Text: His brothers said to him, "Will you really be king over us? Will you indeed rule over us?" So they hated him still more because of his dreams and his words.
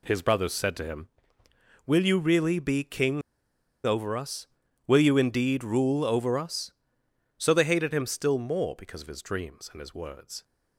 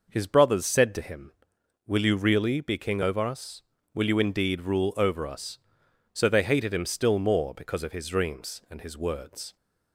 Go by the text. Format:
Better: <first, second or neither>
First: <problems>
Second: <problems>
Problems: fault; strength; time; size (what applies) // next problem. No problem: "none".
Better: second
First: pauses between "king" and "over"; noticeable; at 3.2 s; 0.65 s long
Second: none